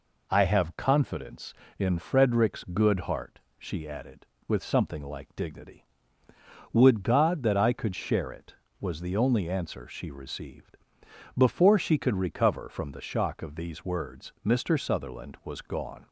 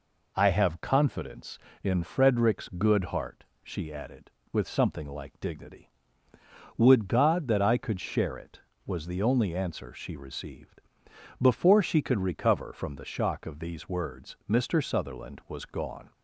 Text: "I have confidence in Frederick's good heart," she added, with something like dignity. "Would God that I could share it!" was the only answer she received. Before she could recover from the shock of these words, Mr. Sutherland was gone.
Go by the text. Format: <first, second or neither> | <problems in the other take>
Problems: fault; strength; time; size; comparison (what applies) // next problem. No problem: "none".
neither | none